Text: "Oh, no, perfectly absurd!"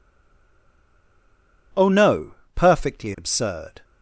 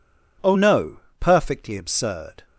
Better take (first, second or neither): second